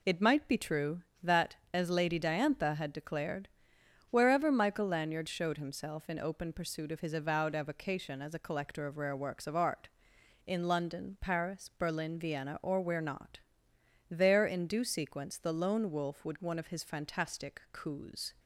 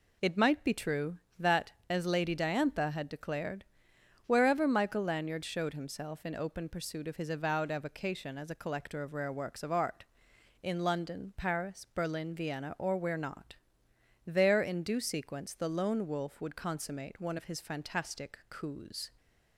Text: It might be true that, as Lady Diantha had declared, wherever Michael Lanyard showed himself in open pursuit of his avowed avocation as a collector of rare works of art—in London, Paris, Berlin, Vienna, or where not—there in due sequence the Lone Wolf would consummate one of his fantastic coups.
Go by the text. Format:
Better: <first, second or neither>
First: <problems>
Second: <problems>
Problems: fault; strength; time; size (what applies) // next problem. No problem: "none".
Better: second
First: skips "consummate"; at 16.4 s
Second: none